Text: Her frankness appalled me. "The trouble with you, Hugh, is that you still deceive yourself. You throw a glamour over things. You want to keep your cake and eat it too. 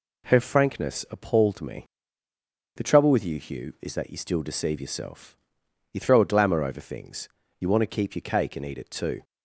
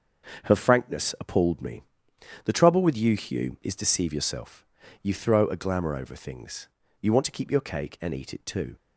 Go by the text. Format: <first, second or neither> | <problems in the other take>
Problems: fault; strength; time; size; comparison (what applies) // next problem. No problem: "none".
first | starts louder than the rest; until 1.5 s; 6.5 dB // skips "that you still"; at 3.7 s